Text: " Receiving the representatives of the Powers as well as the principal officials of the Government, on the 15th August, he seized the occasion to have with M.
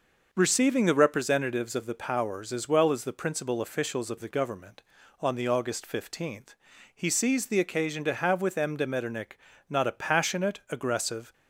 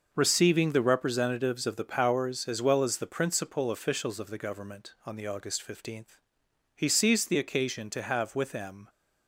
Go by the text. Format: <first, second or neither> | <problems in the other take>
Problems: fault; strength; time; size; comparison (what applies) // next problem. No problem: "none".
second | goes on to say "de Metternich not a passionate aggressive"; strong; from 8.7 s on; 2.5 s long